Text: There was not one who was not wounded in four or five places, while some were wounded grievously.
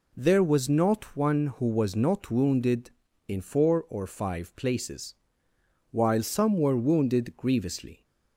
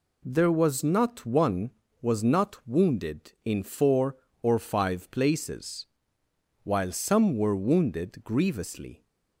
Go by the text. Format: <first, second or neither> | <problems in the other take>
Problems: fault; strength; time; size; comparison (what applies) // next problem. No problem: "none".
first | skips "who"; at 1.8 s